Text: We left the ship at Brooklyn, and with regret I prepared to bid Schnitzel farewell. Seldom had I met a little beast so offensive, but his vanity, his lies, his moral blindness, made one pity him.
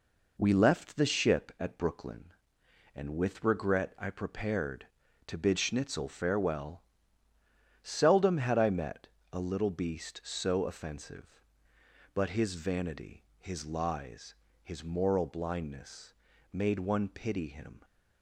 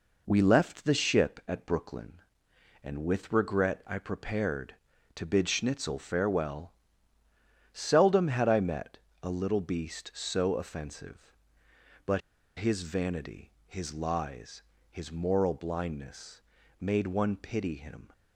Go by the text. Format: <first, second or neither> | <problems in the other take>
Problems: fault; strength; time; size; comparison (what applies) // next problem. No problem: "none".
first | pauses between "met" and "a"; slight; at 8.9 s; 0.24 s long; slight in the first // pauses between "but" and "his"; at 12.2 s; 0.37 s long